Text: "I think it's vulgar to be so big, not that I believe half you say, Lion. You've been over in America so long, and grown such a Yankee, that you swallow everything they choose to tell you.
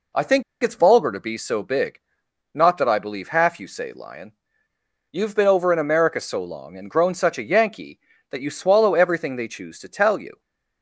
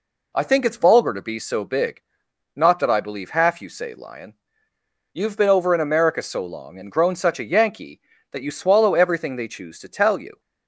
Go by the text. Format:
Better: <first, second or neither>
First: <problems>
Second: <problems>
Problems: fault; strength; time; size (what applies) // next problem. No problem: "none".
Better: second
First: pauses between "think" and "it's"; slight; at 0.4 s; 0.21 s long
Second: none